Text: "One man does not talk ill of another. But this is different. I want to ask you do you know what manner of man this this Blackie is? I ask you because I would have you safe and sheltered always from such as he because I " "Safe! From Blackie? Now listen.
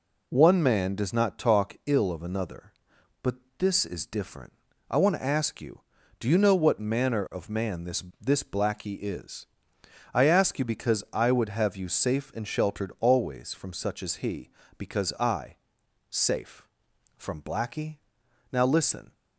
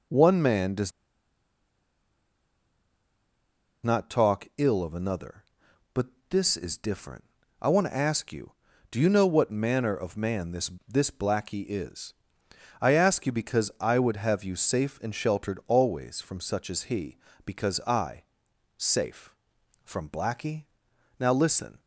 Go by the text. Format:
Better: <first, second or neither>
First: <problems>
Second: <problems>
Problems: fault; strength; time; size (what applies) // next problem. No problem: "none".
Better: first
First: pauses between "But" and "this"; slight; at 3.3 s; 0.24 s long // pauses between "this" and "this"; slight; at 8.0 s; 0.18 s long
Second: pauses between "does" and "not"; strong; at 0.9 s; 2.9 s long // pauses between "But" and "this"; slight; at 6.0 s; 0.24 s long // pauses between "this" and "this"; slight; at 10.6 s; 0.18 s long